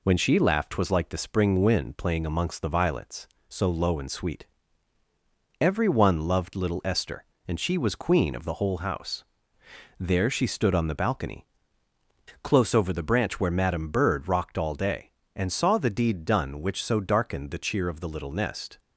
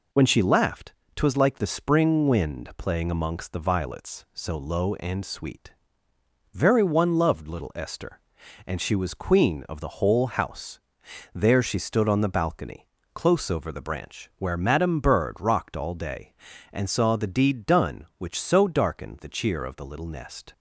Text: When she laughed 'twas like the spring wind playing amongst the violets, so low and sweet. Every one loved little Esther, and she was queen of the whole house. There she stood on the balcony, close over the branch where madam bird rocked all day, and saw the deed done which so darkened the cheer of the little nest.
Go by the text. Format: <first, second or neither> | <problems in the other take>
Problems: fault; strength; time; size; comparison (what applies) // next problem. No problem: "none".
first | pauses between "laughed" and "twas"; slight; at 0.9 s; 0.24 s long // says "Very" for "Every"; at 6.5 s